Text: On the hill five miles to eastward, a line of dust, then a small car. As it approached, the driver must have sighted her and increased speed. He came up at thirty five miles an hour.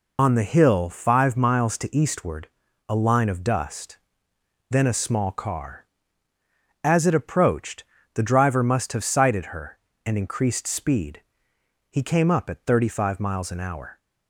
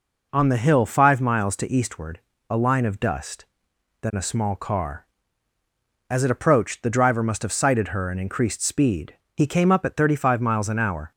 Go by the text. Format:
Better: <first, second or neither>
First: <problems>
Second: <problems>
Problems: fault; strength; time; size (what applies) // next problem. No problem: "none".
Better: second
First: loses the start of "On"; at 0.1 s; 45 ms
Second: none